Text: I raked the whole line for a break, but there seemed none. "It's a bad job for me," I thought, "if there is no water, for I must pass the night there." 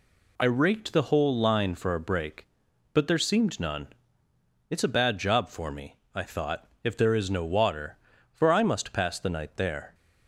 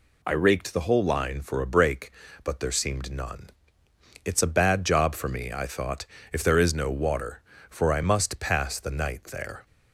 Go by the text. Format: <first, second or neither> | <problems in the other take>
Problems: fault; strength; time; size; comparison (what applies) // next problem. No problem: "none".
second | changes voice at "raked"; from 0.4 s on; 9.5 s long